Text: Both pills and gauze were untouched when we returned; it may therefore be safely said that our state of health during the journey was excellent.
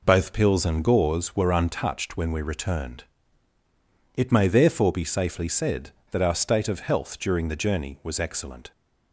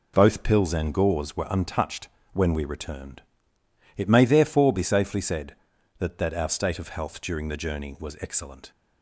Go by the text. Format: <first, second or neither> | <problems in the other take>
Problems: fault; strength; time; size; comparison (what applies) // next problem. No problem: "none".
first | pauses between "untouched" and "when"; slight; at 2.0 s; 0.26 s long // says "that" twice; at 6.1 s